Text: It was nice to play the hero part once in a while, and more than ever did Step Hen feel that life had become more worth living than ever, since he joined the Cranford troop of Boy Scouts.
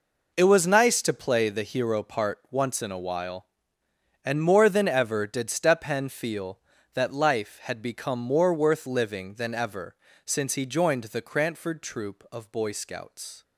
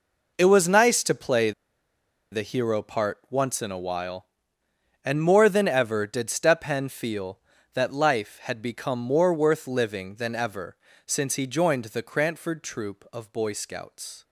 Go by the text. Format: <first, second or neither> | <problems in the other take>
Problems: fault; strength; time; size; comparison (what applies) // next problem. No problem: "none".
first | pauses between "play" and "the"; noticeable; at 1.5 s; 0.80 s long